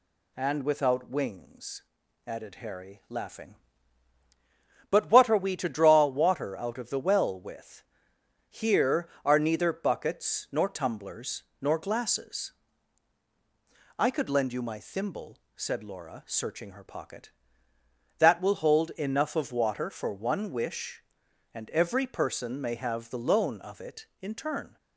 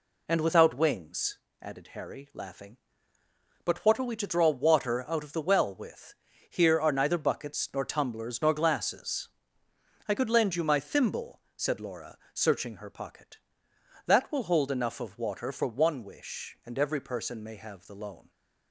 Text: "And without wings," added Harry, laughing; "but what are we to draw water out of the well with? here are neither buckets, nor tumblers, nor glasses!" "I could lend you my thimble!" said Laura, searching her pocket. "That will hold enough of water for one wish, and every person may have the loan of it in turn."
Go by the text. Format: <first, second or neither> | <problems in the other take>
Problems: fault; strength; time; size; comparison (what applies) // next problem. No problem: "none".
first | stops before "of it in turn"; at 18.2 s